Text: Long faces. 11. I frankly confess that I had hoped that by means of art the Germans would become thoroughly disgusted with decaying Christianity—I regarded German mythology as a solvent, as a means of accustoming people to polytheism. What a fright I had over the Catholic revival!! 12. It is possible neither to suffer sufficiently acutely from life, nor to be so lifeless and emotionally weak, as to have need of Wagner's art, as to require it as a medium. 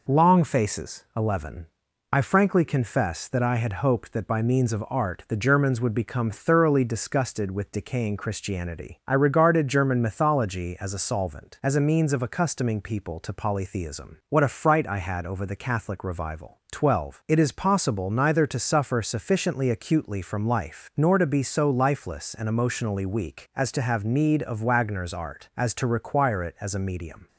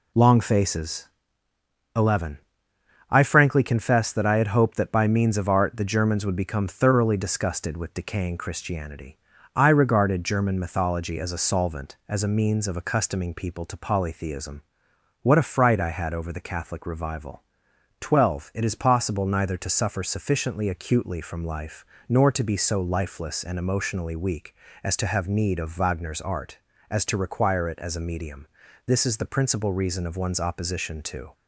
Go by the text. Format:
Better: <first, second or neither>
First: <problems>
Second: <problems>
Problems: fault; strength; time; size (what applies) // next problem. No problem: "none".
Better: first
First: none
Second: goes on to say "This is the principal reason of one's opposition to"; strong; from 28.8 s on; 2.4 s long